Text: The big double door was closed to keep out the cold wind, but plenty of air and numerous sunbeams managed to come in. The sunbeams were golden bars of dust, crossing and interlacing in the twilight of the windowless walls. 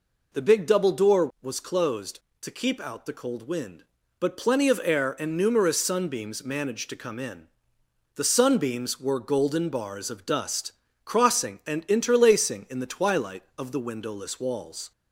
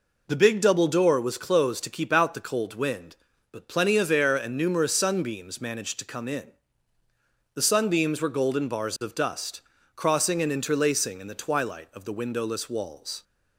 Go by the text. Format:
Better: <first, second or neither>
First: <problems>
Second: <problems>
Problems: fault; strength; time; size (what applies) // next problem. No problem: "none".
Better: neither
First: none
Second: none